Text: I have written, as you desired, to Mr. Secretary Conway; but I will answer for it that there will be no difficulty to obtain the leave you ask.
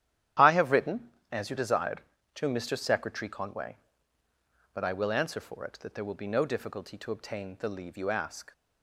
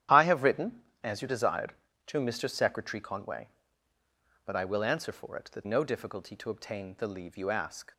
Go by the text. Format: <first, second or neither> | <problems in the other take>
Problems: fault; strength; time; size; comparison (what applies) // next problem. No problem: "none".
first | starts louder than the rest; strong; until 1.4 s; 11 dB; strong in the first // skips "there will be"; at 5.6 s